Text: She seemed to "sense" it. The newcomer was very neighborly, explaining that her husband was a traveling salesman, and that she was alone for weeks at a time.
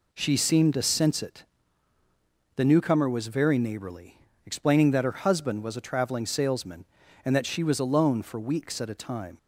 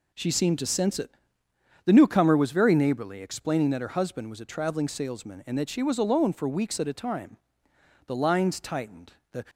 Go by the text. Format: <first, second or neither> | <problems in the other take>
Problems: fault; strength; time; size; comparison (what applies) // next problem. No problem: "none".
first | goes on to say "The lines tightened The"; from 8.0 s on; 1.3 s long